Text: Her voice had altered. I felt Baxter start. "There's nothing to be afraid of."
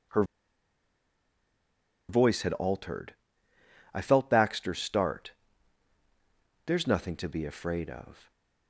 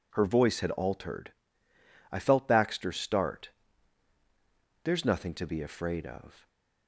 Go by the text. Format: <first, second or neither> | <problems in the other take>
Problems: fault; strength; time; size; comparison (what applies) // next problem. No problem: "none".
second | pauses between "Her" and "voice"; strong; at 0.2 s; 1.8 s long